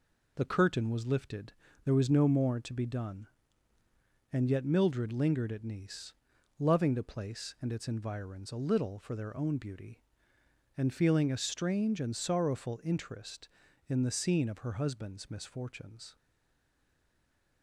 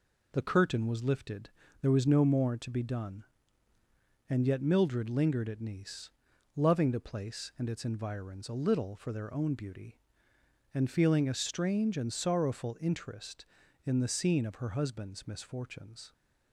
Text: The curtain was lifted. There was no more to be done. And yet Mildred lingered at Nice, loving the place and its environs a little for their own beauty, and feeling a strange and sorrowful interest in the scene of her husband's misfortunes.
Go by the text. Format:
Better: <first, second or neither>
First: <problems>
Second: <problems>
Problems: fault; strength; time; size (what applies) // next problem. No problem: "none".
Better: second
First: stays silent after the last word; noticeable; from 16.1 s on; 1.5 s long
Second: none